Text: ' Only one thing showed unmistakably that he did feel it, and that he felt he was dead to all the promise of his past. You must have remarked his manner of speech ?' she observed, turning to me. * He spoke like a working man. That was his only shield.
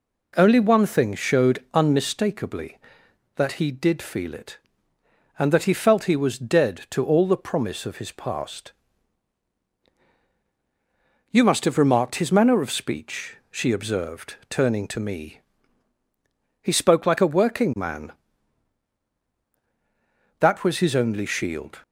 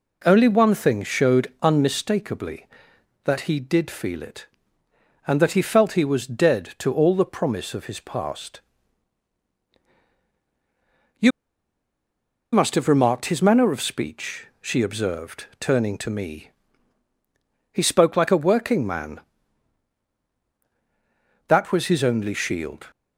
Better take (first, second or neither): first